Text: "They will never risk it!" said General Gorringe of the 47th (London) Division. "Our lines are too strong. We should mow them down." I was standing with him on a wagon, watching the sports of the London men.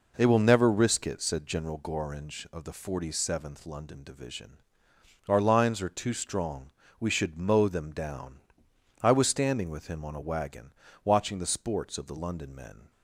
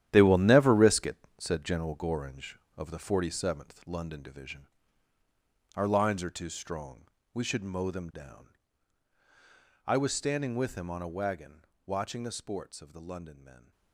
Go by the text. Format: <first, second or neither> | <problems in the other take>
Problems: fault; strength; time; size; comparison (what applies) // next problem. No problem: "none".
first | gets quieter; strong; throughout; 11 dB